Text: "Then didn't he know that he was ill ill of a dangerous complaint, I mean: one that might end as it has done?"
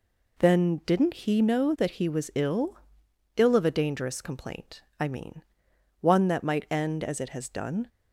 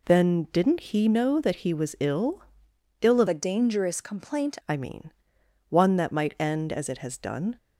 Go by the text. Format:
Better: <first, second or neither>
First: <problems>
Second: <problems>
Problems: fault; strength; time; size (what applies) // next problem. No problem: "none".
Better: first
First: pauses between "ill" and "ill"; noticeable; at 2.7 s; 0.62 s long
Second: pauses between "ill" and "ill"; noticeable; at 2.4 s; 0.62 s long // changes voice from "a" to "complaint"; from 3.2 to 4.5 s; 1.3 s long